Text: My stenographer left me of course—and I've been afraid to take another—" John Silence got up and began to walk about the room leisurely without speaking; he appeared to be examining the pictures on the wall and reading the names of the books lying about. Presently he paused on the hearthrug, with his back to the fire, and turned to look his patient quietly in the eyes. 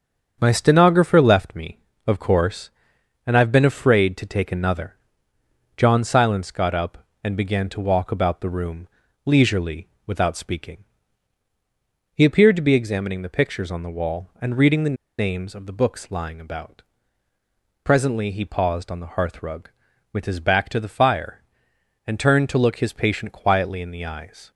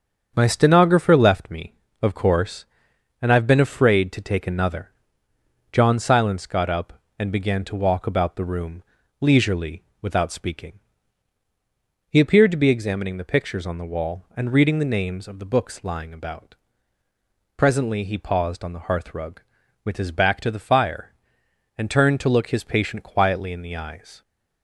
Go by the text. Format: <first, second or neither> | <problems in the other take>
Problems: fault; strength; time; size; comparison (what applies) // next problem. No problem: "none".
second | starts louder than the rest; strong; until 1.4 s; 7.5 dB; strong in the second // pauses between "room" and "leisurely"; at 8.8 s; 0.38 s long; also in the second // pauses between "leisurely" and "without"; slight; at 9.8 s; 0.18 s long; slight in the second // pauses between "the" and "names"; slight; at 14.9 s; 0.24 s long